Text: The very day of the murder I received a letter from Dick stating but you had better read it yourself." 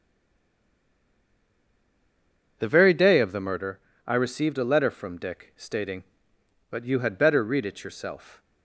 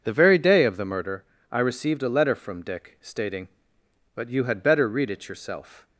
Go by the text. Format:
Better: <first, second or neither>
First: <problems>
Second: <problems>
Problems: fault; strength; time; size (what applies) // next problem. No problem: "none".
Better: second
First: stays silent before the first word; strong; until 2.5 s; 2.5 s long // pauses between "murder" and "I"; slight; at 3.7 s; 0.28 s long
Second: pauses between "murder" and "I"; slight; at 1.2 s; 0.28 s long